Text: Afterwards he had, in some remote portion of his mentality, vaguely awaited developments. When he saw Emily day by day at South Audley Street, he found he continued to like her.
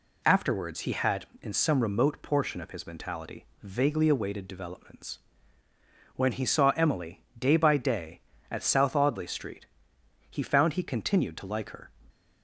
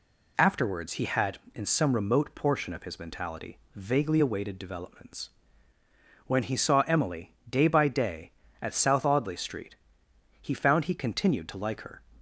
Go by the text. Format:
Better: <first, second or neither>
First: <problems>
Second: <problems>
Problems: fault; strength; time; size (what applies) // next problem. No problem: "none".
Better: neither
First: none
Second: none